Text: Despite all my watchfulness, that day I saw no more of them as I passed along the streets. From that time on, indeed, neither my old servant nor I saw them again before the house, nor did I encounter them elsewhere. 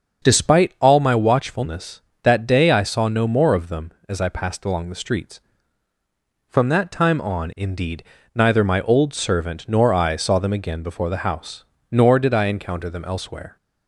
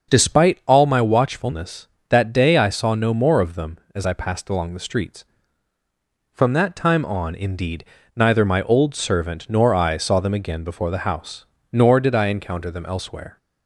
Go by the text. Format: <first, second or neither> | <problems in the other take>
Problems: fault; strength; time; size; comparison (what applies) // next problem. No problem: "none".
neither | starts louder than the rest; the same in both